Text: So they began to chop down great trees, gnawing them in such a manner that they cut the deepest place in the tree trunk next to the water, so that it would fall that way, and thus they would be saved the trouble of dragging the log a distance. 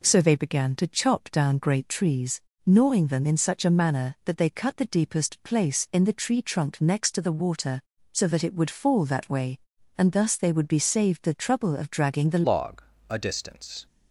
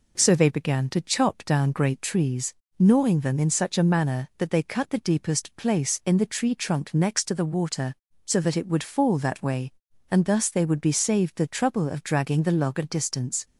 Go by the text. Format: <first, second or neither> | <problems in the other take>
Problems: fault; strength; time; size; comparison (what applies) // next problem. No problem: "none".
second | changes voice at "log"; from 12.4 s on; 1.4 s long // pauses between "log" and "a"; slight; at 12.8 s; 0.28 s long